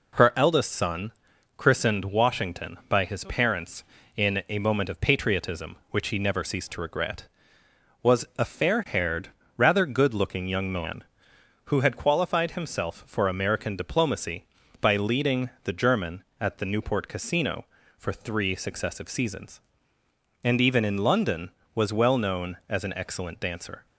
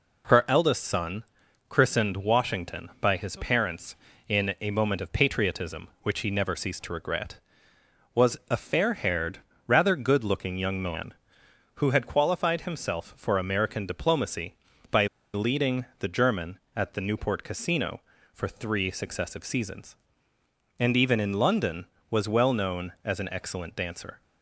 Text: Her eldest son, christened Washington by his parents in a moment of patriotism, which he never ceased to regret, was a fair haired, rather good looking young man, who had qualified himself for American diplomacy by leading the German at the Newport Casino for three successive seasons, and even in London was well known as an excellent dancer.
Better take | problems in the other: first | pauses between "by" and "leading"; slight; at 15.0 s; 0.27 s long

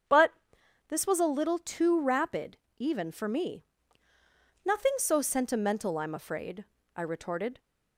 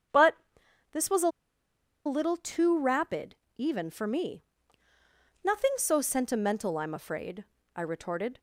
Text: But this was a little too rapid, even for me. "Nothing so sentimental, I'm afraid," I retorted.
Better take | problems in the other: first | starts louder than the rest; strong; until 2.4 s; 7.5 dB; strong in the first // pauses between "But" and "this"; noticeable; at 0.3 s; 0.56 s long; noticeable in the first // pauses between "a" and "little"; noticeable; at 1.2 s; 0.75 s long

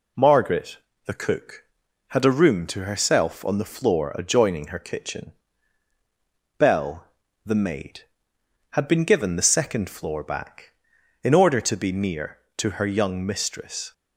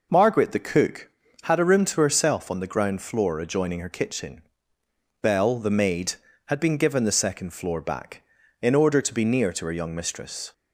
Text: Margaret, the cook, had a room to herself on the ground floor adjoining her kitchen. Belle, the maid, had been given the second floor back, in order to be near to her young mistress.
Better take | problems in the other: second | skips "ground"; at 3.7 s

